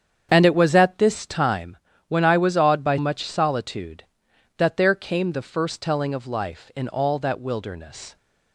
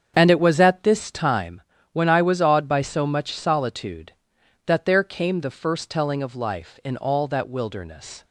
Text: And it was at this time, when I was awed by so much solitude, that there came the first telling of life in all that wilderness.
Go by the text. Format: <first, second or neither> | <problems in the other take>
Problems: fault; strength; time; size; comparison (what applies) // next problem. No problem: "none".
second | starts louder than the rest; strong; until 1.3 s; 8 dB; strong in the second // skips "so"; at 2.9 s